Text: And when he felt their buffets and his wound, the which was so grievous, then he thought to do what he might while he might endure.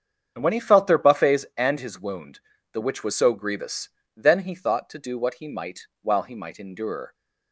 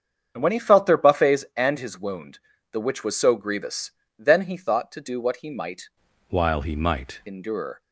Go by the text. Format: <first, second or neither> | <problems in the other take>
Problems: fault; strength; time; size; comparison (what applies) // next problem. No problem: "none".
first | starts louder than the rest; strong; until 1.3 s; 7.5 dB; strong in the first // changes voice from "while" to "might"; from 6.2 to 7.1 s; 0.9 s long